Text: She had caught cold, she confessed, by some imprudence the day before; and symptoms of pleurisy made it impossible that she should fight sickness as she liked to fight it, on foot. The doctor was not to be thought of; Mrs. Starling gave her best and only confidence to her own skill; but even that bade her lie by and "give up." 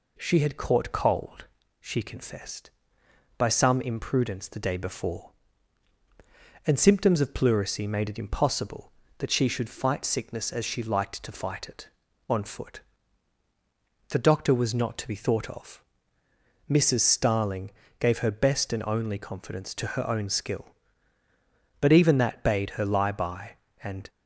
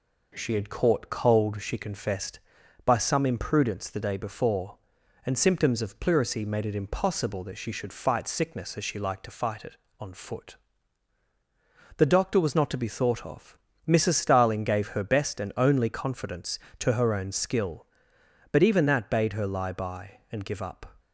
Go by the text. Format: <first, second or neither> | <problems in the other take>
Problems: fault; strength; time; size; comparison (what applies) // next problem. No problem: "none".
second | pauses between "Starling" and "gave"; slight; at 17.6 s; 0.30 s long // stops before "give up"; at 24.0 s